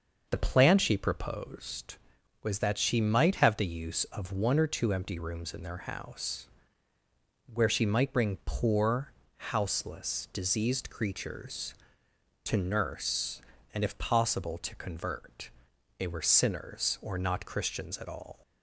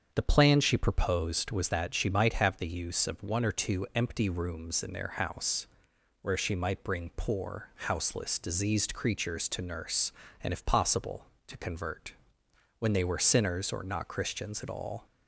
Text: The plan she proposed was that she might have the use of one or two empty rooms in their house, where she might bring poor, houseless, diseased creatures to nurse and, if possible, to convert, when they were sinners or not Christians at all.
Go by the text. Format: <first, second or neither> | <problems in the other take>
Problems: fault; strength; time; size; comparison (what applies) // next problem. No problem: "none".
second | starts louder than the rest; until 1.3 s; 6 dB; strong in the second // skips "when"; at 15.7 s